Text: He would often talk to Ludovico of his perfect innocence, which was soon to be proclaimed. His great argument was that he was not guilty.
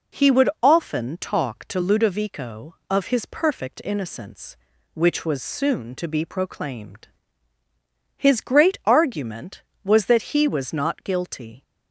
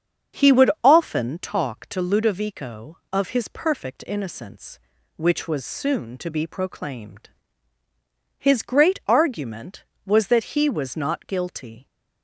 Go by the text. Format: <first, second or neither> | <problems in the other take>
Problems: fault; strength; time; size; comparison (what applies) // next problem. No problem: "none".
first | starts louder than the rest; strong; until 1.4 s; 7 dB